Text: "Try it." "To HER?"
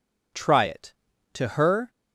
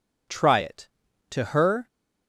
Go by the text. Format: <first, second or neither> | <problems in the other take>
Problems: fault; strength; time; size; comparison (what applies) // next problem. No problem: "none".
neither | none